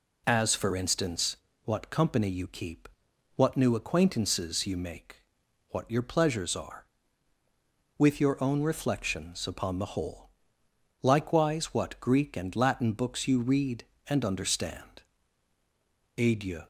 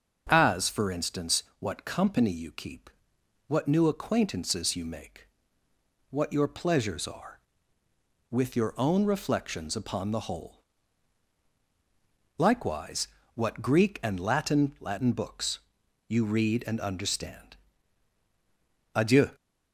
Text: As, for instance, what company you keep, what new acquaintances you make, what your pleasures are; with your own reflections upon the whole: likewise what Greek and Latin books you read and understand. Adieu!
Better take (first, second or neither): first